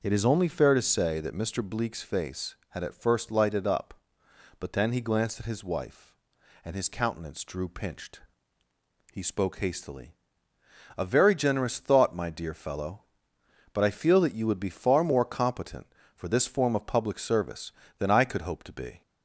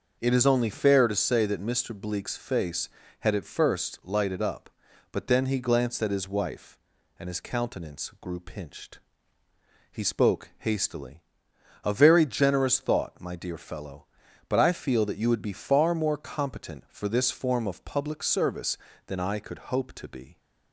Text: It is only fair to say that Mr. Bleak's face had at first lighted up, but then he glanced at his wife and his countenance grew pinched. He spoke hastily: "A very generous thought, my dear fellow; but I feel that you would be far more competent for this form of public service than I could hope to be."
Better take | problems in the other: second | starts louder than the rest; noticeable; until 1.0 s; 6 dB // says "drew" for "grew"; at 7.4 s

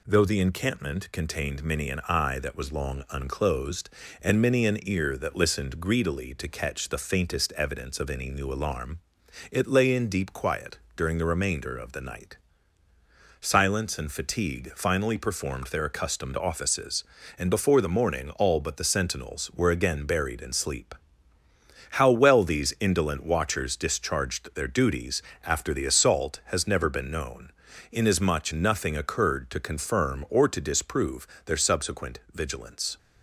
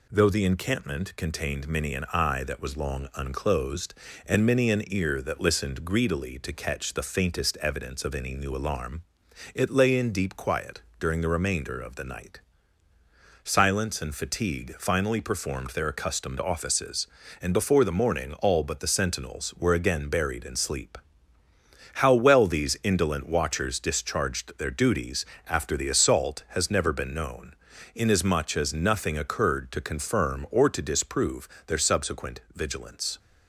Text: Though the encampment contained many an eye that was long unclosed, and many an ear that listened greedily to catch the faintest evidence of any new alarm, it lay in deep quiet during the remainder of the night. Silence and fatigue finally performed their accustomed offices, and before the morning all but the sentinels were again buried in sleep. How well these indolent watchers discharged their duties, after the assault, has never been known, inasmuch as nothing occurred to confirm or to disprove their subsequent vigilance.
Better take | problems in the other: second | pauses between "quiet" and "during"; slight; at 10.7 s; 0.16 s long; slight in the second // skips "as"; at 28.5 s // pauses between "disprove" and "their"; slight; at 31.2 s; 0.20 s long; slight in the second

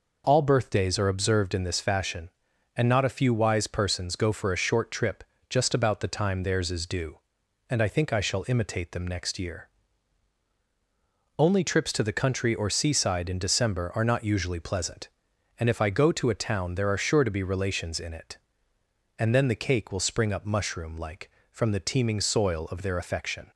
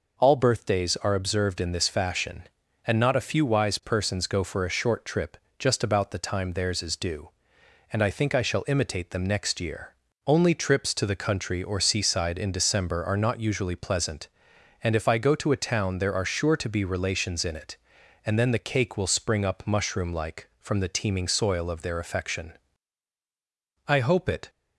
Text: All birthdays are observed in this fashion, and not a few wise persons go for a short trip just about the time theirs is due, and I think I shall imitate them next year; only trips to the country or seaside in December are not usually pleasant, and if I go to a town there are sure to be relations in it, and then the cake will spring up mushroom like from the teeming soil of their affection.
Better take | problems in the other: first | pauses between "trip" and "just"; slight; at 5.3 s; 0.20 s long; slight in the first // goes on to say "I hope it"; noticeable; from 23.8 s on; 0.62 s long

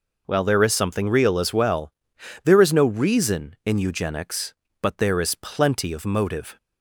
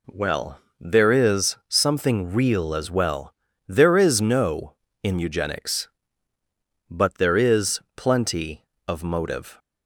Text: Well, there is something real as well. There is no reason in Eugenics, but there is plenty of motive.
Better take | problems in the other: first | skips "reason"; at 4.8 s // pauses between "is" and "plenty"; slight; at 7.8 s; 0.16 s long

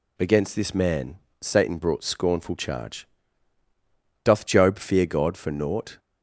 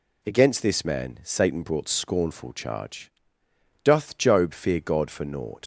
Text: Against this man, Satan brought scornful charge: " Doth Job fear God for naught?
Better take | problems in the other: first | leaves "naught" unfinished; at 5.6 s; 125 ms

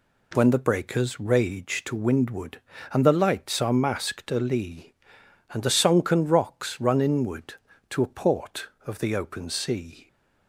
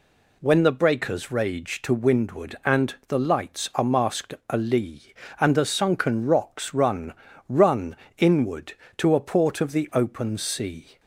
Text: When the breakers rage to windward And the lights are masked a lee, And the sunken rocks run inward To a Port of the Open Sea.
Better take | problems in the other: first | says "run" twice; at 7.4 s

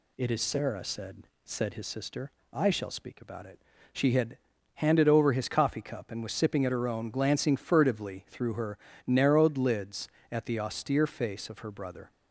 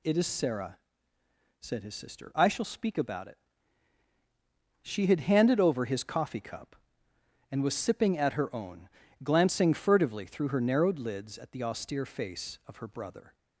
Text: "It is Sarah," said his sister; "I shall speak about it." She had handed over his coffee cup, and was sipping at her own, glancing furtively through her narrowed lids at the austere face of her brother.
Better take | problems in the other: second | says "said" twice; at 1.4 s // pauses between "had" and "handed"; slight; at 4.3 s; 0.36 s long // pauses between "her" and "narrowed"; slight; at 8.7 s; 0.30 s long

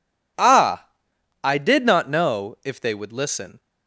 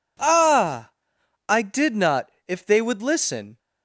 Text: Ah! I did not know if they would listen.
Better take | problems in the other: first | skips "know"; at 2.3 s

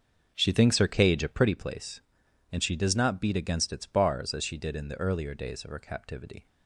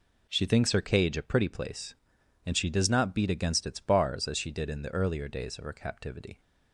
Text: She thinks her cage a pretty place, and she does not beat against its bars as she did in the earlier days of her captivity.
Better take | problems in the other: second | starts louder than the rest; until 1.7 s; 6 dB

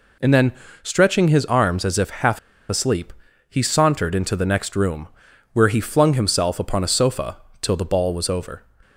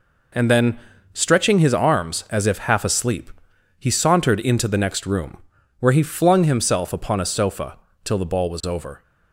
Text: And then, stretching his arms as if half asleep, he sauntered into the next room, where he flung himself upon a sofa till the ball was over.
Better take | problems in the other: second | pauses between "half" and "asleep"; slight; at 2.3 s; 0.30 s long // pauses between "sofa" and "till"; slight; at 7.3 s; 0.24 s long; slight in the second

